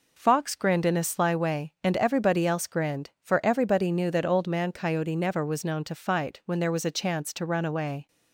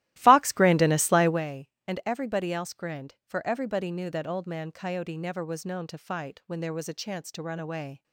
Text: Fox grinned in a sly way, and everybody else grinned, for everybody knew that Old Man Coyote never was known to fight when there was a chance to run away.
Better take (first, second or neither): first